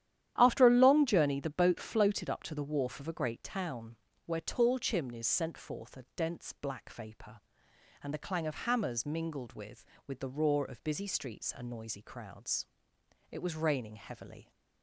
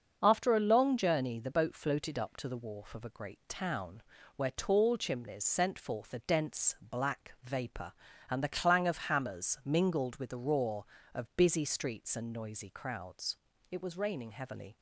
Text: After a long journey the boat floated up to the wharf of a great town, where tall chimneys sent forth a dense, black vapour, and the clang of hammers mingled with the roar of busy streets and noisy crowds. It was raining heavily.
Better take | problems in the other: second | starts louder than the rest; strong; until 1.3 s; 11 dB; also in the second // says "with" twice; at 10.0 s

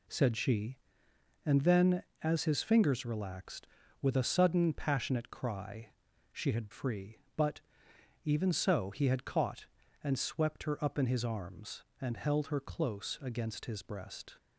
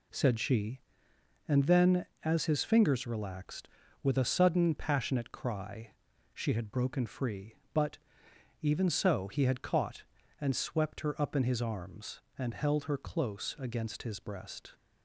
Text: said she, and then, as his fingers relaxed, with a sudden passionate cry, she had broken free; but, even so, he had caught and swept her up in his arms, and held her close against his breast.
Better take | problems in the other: second | skips "broken"; at 6.7 s

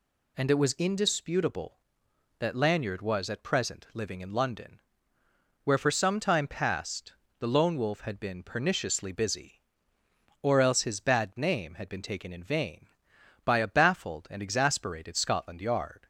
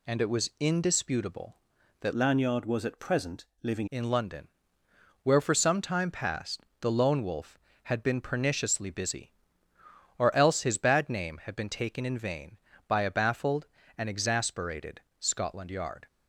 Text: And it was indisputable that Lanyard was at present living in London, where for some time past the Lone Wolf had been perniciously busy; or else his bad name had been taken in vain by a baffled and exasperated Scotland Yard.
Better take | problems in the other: first | changes voice from "Lanyard" to "living"; from 2.1 to 3.8 s; 1.7 s long // pauses between "present" and "living"; slight; at 3.4 s; 0.18 s long // pauses between "past" and "the"; slight; at 6.6 s; 0.20 s long; slight in the first // pauses between "exasperated" and "Scotland"; slight; at 15.0 s; 0.18 s long

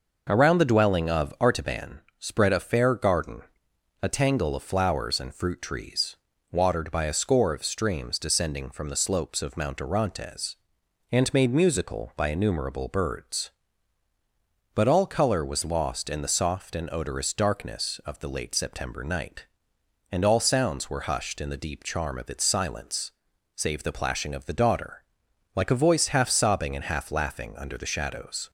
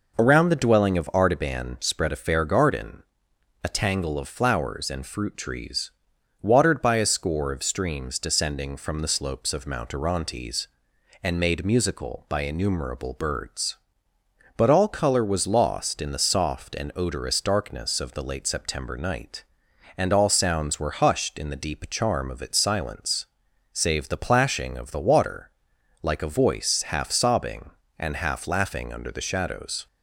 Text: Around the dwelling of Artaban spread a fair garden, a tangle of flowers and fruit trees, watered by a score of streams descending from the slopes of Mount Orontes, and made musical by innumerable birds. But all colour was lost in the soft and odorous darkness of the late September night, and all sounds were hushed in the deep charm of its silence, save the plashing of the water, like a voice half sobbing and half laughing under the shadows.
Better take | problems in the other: second | pauses between "Artaban" and "spread"; slight; at 2.0 s; 0.18 s long // says "daughter" for "water"; at 24.5 s

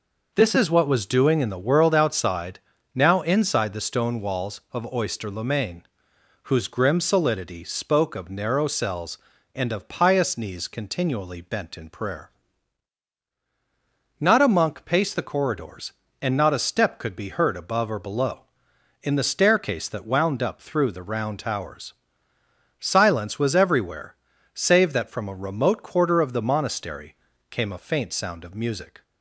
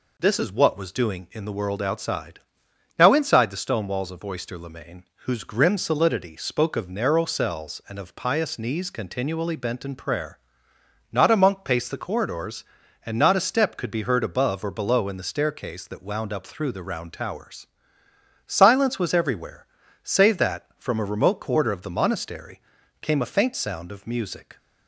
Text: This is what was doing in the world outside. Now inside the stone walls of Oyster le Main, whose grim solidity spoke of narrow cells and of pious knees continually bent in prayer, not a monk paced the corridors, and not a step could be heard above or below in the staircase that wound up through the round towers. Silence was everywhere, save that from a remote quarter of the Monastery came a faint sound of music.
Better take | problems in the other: neither | pauses between "Monastery" and "came"; the same in both

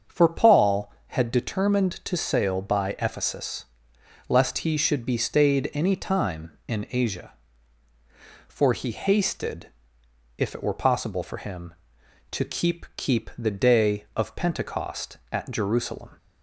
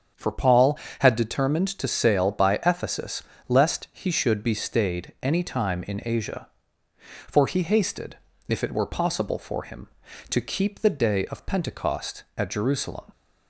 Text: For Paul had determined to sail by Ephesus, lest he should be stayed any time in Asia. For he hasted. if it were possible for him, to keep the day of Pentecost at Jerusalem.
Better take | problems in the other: second | starts louder than the rest; until 1.2 s; 6.5 dB; strong in the second // says "keep" twice; at 12.9 s

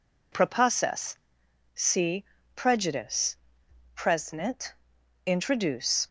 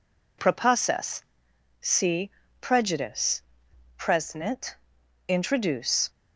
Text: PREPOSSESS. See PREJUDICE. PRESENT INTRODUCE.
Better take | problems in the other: neither | pauses between "See" and "PREJUDICE"; slight; the same in both // pauses between "PRESENT" and "INTRODUCE"; noticeable; the same in both

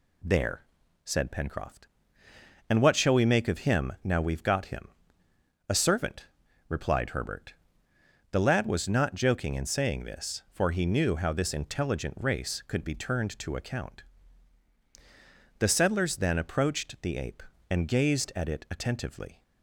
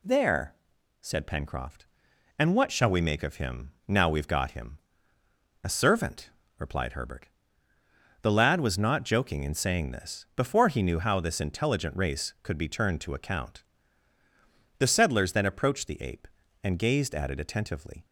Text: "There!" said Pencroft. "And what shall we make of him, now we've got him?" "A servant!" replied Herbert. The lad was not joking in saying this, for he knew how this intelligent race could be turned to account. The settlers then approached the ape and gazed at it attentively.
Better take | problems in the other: first | says "before" for "for"; at 10.3 s

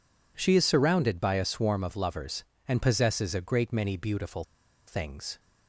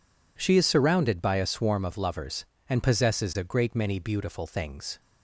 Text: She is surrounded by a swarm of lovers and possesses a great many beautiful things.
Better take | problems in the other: second | pauses between "beautiful" and "things"; at 4.4 s; 0.43 s long

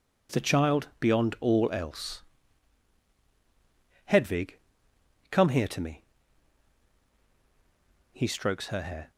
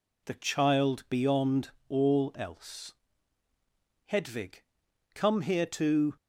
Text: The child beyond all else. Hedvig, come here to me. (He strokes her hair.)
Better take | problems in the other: first | pauses between "beyond" and "all"; slight; at 1.7 s; 0.18 s long // stops before "me He strokes her hair"; at 6.1 s

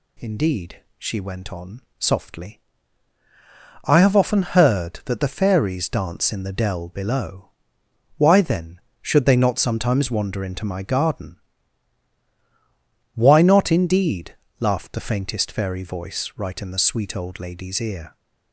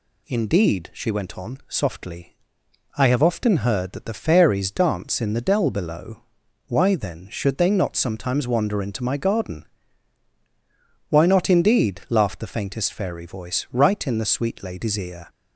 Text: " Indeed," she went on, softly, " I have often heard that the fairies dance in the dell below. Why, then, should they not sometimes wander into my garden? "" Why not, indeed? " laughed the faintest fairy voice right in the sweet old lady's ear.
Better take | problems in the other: first | skips "old"; at 14.6 s

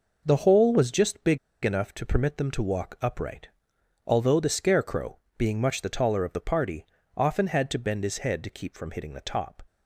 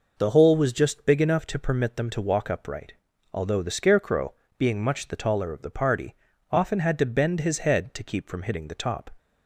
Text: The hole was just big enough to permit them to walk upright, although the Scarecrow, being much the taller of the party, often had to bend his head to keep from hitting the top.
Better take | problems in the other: second | pauses between "big" and "enough"; slight; at 1.3 s; 0.26 s long

